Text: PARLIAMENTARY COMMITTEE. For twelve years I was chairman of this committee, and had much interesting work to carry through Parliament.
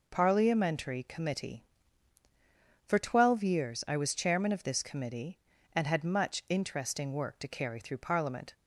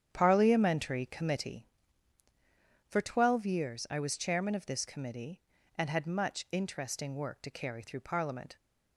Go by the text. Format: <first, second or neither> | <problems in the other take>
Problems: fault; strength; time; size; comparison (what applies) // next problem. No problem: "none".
first | starts louder than the rest; strong; until 1.6 s; 9 dB